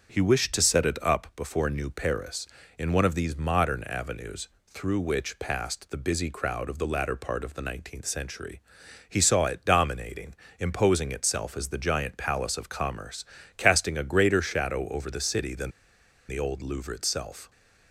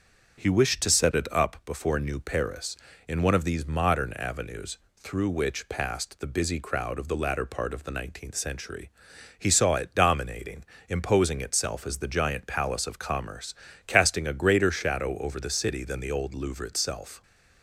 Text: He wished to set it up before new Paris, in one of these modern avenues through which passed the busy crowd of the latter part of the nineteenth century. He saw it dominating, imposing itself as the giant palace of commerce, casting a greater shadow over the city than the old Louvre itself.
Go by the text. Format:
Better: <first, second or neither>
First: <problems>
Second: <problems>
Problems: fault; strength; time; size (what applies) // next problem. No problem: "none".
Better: second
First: starts louder than the rest; until 1.1 s; 7 dB // pauses between "avenues" and "through"; slight; at 4.4 s; 0.18 s long // pauses between "than" and "the"; noticeable; at 15.7 s; 0.58 s long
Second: starts louder than the rest; until 1.4 s; 6.5 dB // pauses between "avenues" and "through"; slight; at 4.7 s; 0.18 s long